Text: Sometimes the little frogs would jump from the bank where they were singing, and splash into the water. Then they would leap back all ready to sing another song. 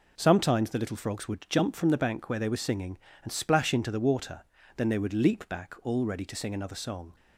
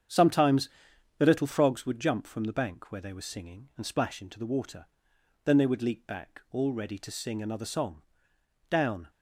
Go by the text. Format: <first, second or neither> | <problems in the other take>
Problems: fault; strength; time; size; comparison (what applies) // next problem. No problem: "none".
first | starts louder than the rest; strong; until 1.6 s; 8 dB // pauses between "Sometimes" and "the"; noticeable; at 0.6 s; 0.50 s long // goes on to say "Down"; slight; from 8.6 s on; 0.40 s long